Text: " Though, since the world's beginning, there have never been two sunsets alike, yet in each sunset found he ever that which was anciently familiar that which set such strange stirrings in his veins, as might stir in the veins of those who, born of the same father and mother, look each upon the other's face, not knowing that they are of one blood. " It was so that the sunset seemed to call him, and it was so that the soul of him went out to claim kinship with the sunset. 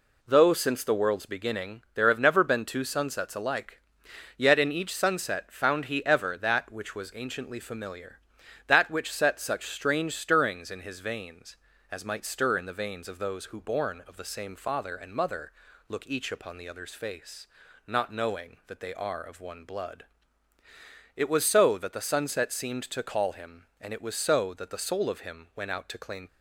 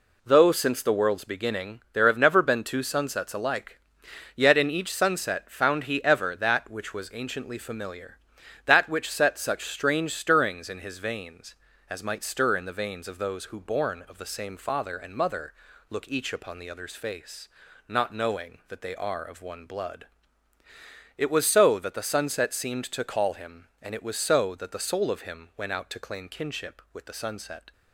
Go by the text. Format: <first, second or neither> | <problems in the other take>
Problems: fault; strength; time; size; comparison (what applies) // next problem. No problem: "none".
second | stops before "kinship with the sunset"; at 26.2 s